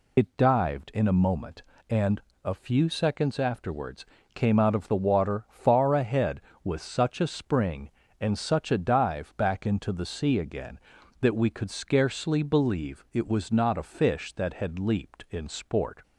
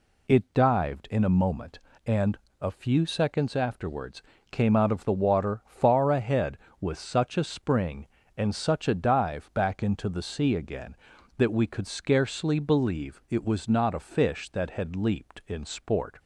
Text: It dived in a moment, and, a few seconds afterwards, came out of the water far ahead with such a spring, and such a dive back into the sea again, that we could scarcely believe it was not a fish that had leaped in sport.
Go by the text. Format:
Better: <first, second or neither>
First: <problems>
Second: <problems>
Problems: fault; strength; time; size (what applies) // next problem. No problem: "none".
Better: second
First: loses the start of "It"; at 0.1 s; 50 ms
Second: none